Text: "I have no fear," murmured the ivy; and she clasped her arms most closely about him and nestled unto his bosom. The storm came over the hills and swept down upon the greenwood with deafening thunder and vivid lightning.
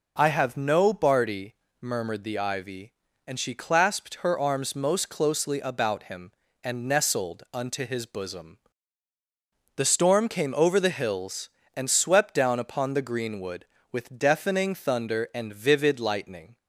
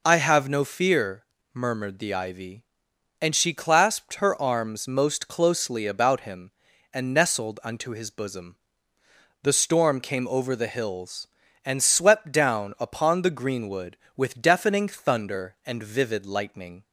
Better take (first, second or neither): second